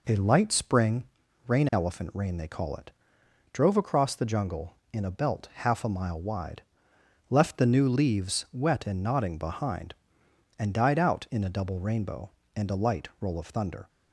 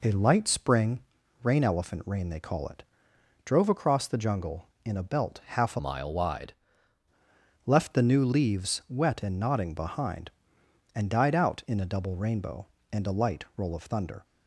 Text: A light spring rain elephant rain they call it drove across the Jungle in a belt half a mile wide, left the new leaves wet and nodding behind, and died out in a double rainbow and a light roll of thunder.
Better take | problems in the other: first | pauses between "spring" and "rain"; at 1.0 s; 0.42 s long; also in the first // pauses between "it" and "drove"; noticeable; at 2.8 s; 0.60 s long; noticeable in the first // changes voice from "mile" to "wide"; from 5.7 to 6.5 s; 0.8 s long

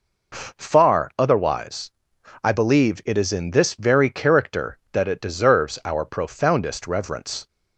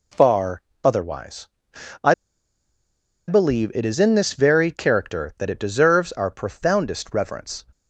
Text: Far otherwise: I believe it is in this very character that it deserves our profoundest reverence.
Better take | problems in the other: first | pauses between "Far" and "otherwise"; slight; at 0.6 s; 0.24 s long // pauses between "I" and "believe"; at 2.1 s; 1.1 s long

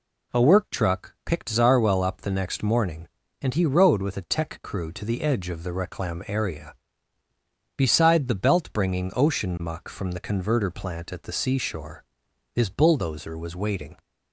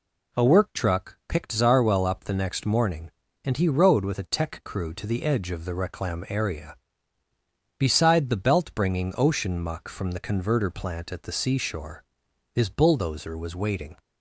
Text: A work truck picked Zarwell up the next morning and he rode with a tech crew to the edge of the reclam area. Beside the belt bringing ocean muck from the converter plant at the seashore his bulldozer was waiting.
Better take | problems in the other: neither | pauses between "seashore" and "his"; noticeable; the same in both

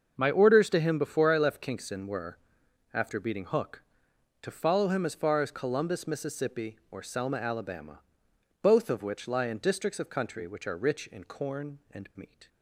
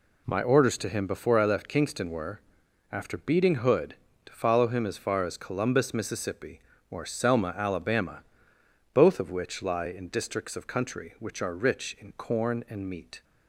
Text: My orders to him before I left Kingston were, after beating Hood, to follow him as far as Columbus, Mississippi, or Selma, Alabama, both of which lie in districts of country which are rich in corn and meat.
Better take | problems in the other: second | starts louder than the rest; until 1.1 s; 6.5 dB // says "Hook" for "Hood"; at 3.4 s

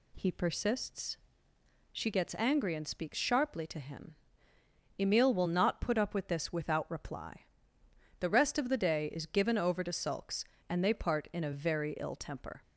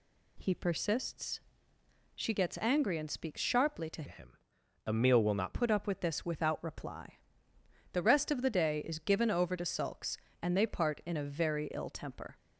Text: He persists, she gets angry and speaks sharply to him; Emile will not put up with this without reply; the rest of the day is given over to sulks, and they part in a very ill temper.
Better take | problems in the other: first | changes voice from "him" to "not"; from 4.0 to 5.5 s; 1.5 s long

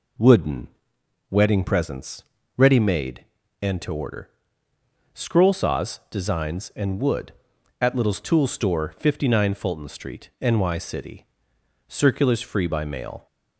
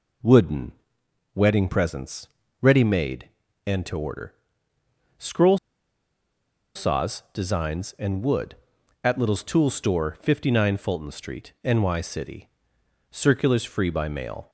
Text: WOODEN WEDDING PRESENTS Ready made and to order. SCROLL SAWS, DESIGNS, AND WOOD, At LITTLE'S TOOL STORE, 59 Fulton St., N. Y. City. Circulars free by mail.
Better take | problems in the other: first | pauses between "WOODEN" and "WEDDING"; noticeable; at 0.7 s; 0.60 s long; noticeable in the first // pauses between "PRESENTS" and "Ready"; slight; at 2.2 s; 0.34 s long; slight in the first // pauses between "SCROLL" and "SAWS"; at 5.5 s; 1.1 s long

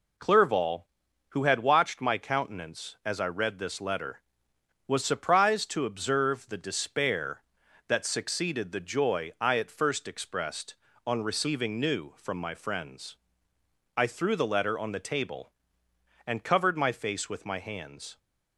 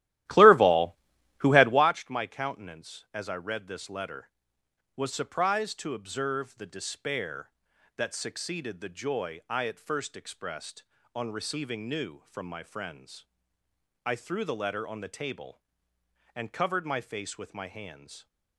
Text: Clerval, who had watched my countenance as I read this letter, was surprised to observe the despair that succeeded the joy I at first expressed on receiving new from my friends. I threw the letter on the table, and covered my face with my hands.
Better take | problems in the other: first | starts louder than the rest; strong; until 2.0 s; 14.5 dB

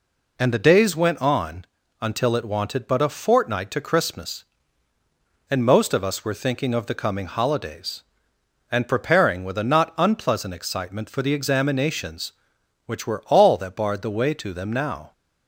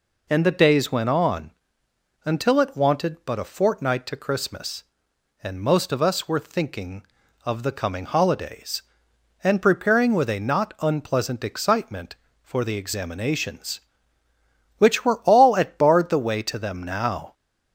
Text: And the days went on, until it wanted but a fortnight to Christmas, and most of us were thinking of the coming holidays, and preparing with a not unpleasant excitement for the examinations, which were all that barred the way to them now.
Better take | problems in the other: first | says "at" for "that"; at 15.5 s

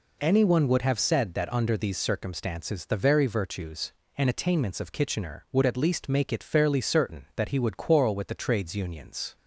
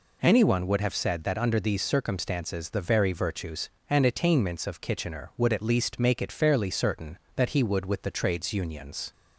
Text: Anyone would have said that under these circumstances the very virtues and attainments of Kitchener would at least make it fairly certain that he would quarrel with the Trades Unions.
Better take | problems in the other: first | skips "quarrel"; at 7.8 s

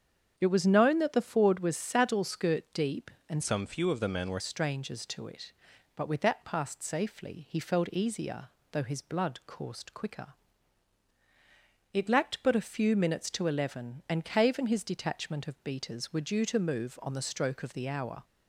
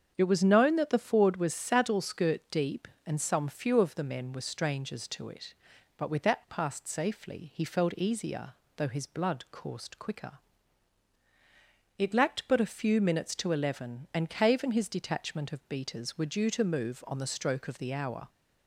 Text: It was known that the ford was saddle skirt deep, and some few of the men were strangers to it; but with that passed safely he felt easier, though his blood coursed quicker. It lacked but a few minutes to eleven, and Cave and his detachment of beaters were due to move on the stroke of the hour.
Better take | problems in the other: second | starts louder than the rest; strong; until 1.3 s; 7.5 dB; strong in the second // changes voice from "some" to "were"; from 3.4 to 4.3 s; 0.9 s long

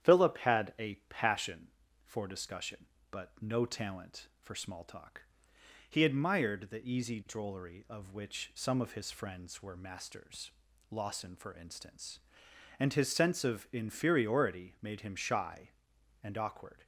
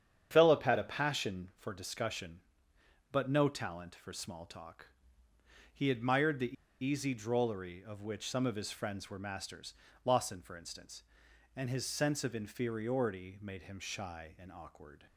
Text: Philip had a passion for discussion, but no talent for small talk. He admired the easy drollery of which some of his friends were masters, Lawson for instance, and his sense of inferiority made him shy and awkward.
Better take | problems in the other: first | starts louder than the rest; strong; until 1.3 s; 8.5 dB; strong in the first // pauses between "the" and "easy"; slight; at 6.5 s; 0.28 s long

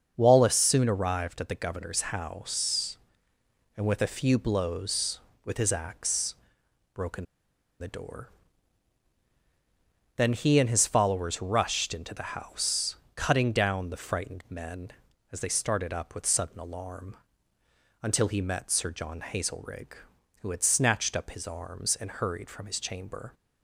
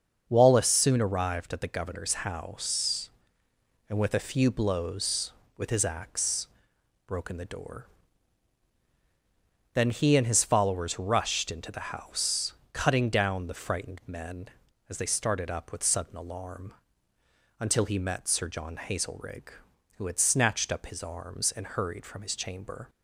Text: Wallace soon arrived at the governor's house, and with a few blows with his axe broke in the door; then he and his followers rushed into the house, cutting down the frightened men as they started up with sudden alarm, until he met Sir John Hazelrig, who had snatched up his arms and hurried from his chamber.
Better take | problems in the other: second | starts louder than the rest; until 1.1 s; 6.5 dB; also in the second // pauses between "axe" and "broke"; noticeable; at 6.3 s; 0.58 s long; noticeable in the second // pauses between "in" and "the"; noticeable; at 7.2 s; 0.55 s long

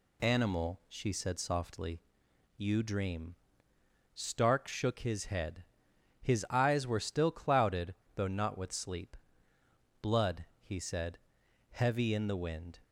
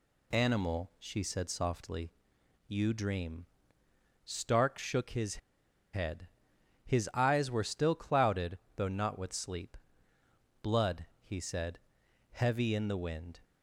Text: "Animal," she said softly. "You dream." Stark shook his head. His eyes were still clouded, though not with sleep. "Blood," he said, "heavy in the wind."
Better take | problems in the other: first | pauses between "his" and "head"; noticeable; at 5.3 s; 0.61 s long

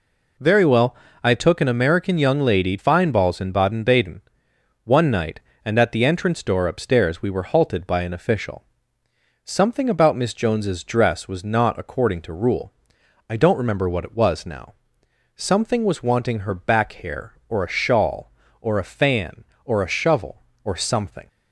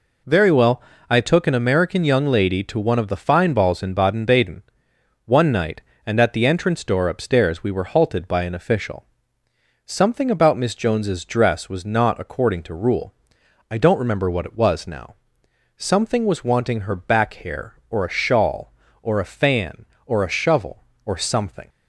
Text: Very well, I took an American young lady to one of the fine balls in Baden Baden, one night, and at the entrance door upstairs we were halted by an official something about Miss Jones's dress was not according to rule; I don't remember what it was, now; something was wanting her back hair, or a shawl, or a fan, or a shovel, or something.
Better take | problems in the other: second | skips "to one of the"; at 2.7 s // pauses between "official" and "something"; noticeable; at 8.6 s; 0.80 s long; noticeable in the second

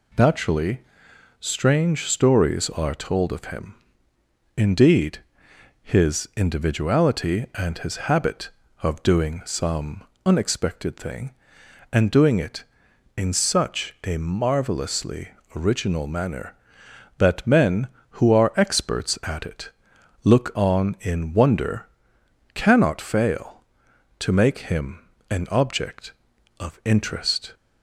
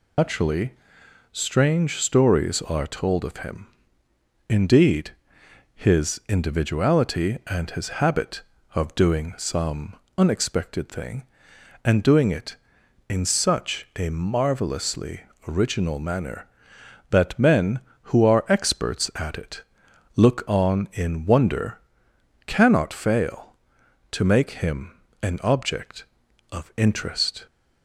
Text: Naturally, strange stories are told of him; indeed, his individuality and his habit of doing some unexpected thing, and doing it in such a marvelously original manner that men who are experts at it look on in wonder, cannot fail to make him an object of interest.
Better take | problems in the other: first | loses the start of "Naturally"; at 0.1 s; 120 ms // pauses between "some" and "unexpected"; slight; at 9.9 s; 0.22 s long; slight in the first // pauses between "marvelously" and "original"; slight; at 15.2 s; 0.26 s long; slight in the first // pauses between "it" and "look"; noticeable; at 19.6 s; 0.54 s long; noticeable in the first // pauses between "him" and "an"; slight; at 24.9 s; 0.30 s long; slight in the first

